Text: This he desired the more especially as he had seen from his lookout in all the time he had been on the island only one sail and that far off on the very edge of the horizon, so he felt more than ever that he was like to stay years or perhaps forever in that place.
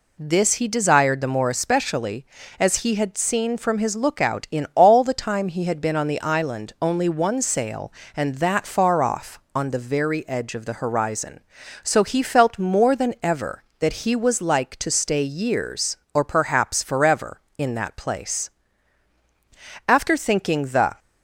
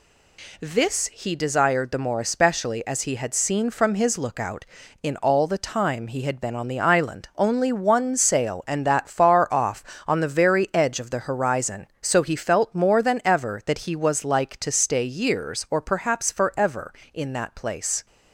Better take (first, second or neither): second